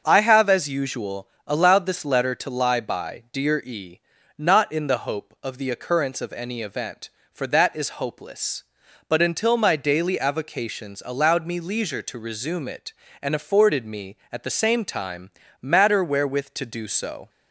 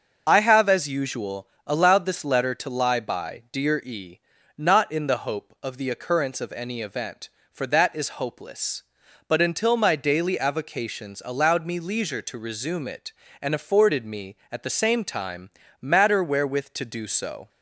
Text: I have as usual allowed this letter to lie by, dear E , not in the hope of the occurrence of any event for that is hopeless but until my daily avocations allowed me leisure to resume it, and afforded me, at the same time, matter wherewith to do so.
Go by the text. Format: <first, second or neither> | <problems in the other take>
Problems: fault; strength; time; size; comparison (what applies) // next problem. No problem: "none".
first | loses the start of "I"; at 0.2 s; 25 ms // starts louder than the rest; until 1.2 s; 6.5 dB; also in the first // pauses between "usual" and "allowed"; slight; at 1.4 s; 0.18 s long; slight in the first